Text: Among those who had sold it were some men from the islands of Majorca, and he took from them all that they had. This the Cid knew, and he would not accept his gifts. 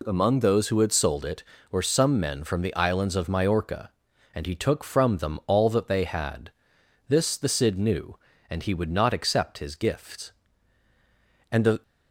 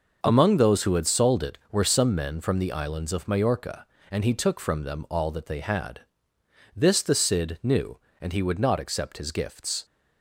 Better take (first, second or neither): second